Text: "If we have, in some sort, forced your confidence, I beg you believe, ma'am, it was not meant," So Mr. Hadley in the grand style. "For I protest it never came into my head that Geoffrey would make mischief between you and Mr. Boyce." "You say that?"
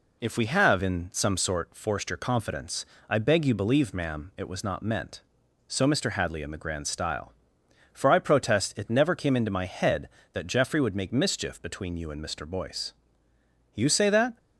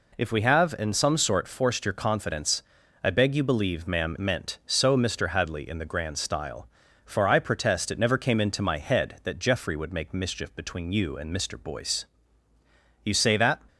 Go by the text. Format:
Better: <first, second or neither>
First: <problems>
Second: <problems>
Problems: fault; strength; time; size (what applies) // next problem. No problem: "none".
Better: first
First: none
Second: skips "it was not"; at 4.1 s